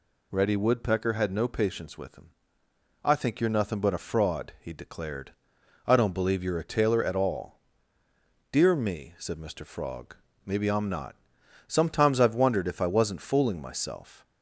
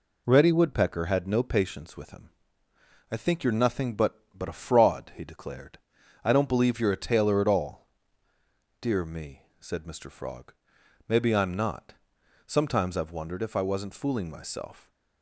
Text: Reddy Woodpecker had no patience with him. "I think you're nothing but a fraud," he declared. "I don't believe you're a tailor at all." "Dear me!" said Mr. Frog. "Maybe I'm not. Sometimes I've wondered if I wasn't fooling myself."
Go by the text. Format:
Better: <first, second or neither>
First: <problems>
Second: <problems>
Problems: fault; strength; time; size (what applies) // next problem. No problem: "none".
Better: first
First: none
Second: says "but" twice; at 4.3 s